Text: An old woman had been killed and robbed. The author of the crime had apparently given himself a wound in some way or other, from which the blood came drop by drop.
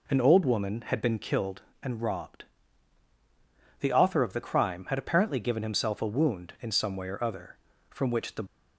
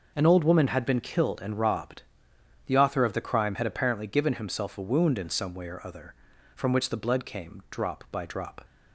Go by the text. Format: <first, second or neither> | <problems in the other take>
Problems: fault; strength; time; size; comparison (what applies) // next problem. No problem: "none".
second | stops before "blood came drop by drop"; at 8.4 s